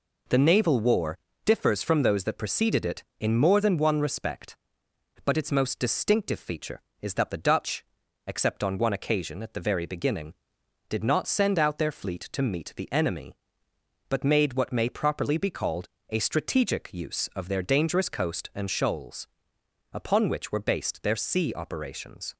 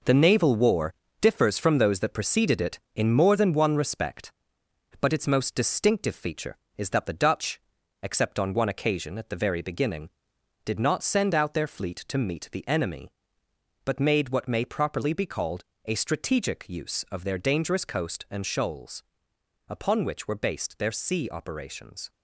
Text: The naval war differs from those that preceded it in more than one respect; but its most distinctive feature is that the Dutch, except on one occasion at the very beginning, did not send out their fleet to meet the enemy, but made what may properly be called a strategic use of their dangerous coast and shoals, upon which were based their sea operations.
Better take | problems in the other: first | gets quieter; strong; throughout; 8.5 dB // pauses between "war" and "differs"; slight; at 0.9 s; 0.28 s long; slight in the first // pauses between "called" and "a"; slight; at 15.6 s; 0.22 s long; slight in the first

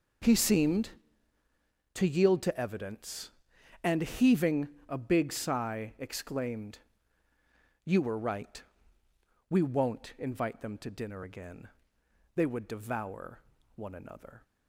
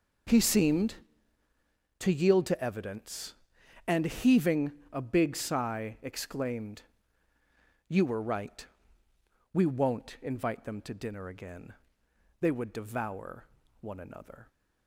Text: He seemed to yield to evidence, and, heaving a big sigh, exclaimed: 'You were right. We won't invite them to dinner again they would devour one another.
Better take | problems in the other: neither | pauses between "heaving" and "a"; slight; the same in both // pauses between "again" and "they"; noticeable; the same in both // pauses between "devour" and "one"; slight; the same in both

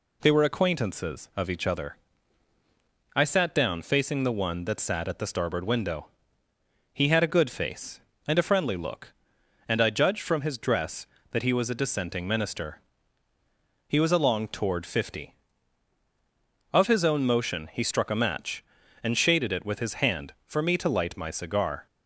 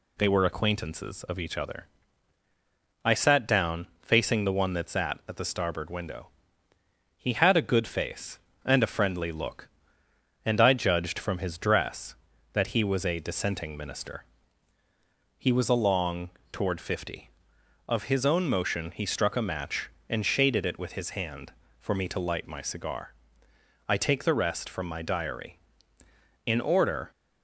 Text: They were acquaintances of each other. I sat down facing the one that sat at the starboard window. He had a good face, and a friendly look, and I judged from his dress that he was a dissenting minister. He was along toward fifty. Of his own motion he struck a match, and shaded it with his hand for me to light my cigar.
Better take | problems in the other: first | pauses between "along" and "toward"; slight; at 16.3 s; 0.22 s long // goes on to say "I take the rest from my diary In order"; strong; from 23.8 s on; 3.2 s long

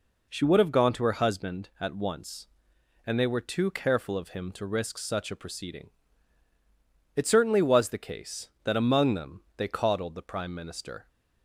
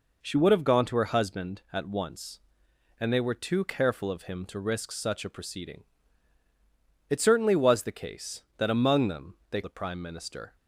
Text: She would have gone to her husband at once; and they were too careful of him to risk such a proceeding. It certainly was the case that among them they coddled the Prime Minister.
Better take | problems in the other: first | pauses between "them" and "they"; slight; at 9.3 s; 0.16 s long; slight in the first // skips "coddled"; at 9.6 s

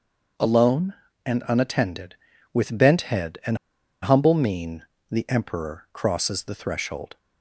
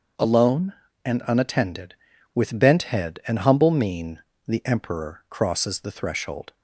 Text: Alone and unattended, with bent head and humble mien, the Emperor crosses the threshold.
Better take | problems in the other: second | starts louder than the rest; noticeable; until 1.7 s; 6 dB; also in the second // pauses between "and" and "humble"; at 3.5 s; 0.45 s long

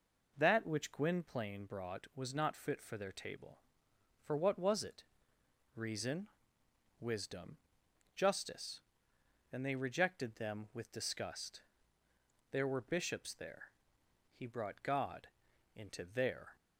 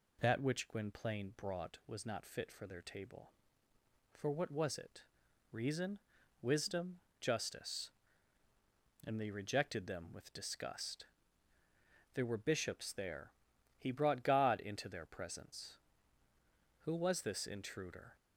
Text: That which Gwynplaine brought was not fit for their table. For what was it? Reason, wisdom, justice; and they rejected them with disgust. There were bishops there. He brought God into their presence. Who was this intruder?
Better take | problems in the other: second | pauses between "God" and "into"; noticeable; at 15.2 s; 0.48 s long // stops before "presence Who was this intruder"; at 16.5 s

